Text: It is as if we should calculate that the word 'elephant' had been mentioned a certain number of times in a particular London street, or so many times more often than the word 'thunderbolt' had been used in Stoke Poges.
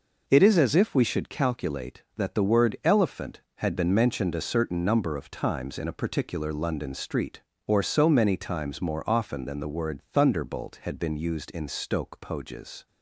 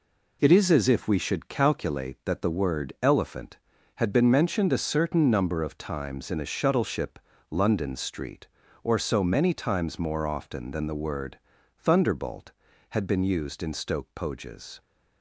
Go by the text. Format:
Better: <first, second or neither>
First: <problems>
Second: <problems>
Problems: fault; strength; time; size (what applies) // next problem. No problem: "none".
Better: first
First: none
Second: says "shuttleship" for "particular"; at 6.4 s // pauses between "word" and "thunderbolt"; at 11.3 s; 0.40 s long